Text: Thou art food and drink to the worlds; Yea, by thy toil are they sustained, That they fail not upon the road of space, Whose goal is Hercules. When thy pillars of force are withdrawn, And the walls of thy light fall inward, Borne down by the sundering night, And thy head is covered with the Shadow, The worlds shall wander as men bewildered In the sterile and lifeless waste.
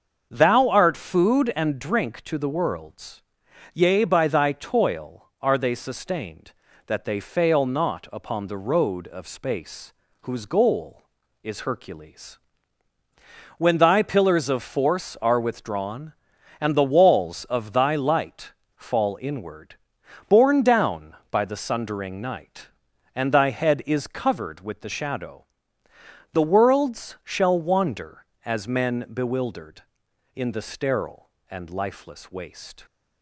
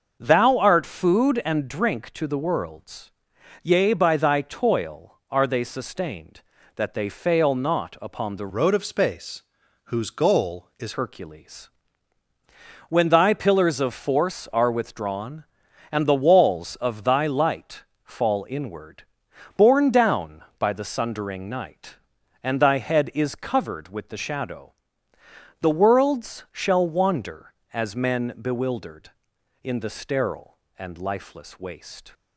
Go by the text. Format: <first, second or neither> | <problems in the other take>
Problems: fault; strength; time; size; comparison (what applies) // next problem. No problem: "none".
first | starts louder than the rest; until 1.2 s; 6.5 dB; also in the first // changes voice from "road" to "is"; from 8.5 to 10.9 s; 2.4 s long // pauses between "light" and "fall"; slight; at 17.8 s; 0.20 s long; slight in the first